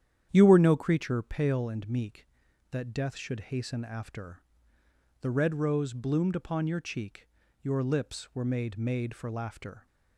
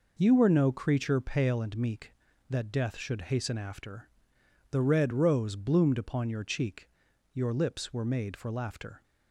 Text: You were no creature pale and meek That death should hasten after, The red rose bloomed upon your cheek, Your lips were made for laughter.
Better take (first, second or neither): second